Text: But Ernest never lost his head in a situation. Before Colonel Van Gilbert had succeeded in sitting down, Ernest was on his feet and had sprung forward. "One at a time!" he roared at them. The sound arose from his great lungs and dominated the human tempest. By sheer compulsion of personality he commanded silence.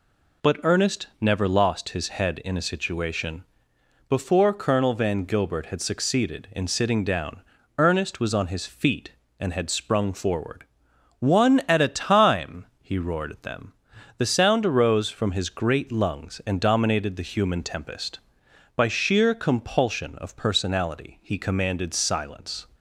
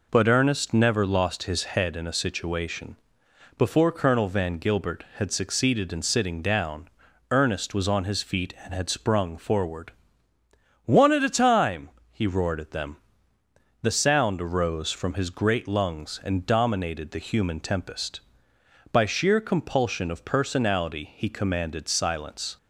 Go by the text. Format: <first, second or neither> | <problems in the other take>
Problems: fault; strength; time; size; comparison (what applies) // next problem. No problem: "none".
neither | none